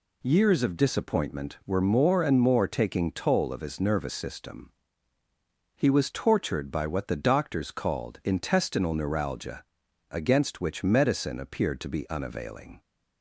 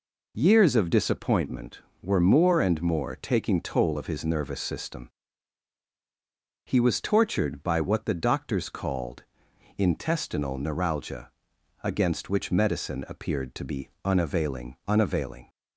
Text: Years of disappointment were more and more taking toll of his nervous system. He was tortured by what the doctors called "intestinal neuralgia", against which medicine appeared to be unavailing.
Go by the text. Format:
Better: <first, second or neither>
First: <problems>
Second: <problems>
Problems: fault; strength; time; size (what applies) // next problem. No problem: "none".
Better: first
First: none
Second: pauses between "called" and "intestinal"; noticeable; at 9.2 s; 0.52 s long // pauses between "be" and "unavailing"; slight; at 13.8 s; 0.16 s long // says "unavailing" twice; at 14.8 s